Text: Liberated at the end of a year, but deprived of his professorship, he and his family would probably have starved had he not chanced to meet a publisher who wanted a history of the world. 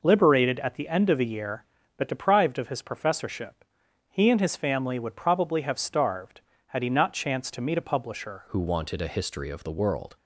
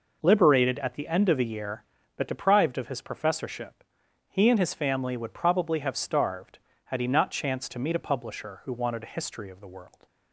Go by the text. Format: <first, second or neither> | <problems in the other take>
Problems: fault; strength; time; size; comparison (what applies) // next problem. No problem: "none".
second | changes voice at "who"; from 8.4 s on; 1.7 s long